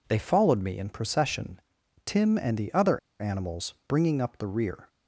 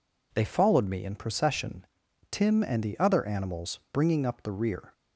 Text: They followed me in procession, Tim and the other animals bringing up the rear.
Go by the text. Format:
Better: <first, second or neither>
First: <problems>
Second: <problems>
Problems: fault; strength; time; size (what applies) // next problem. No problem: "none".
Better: second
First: pauses between "other" and "animals"; slight; at 2.9 s; 0.20 s long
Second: none